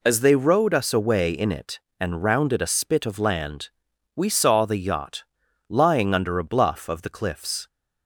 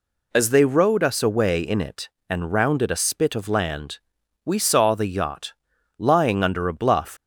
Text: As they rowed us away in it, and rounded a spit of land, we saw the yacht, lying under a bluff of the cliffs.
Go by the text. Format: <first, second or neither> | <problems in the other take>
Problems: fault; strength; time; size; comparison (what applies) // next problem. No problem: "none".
first | stops before "of the cliffs"; at 7.1 s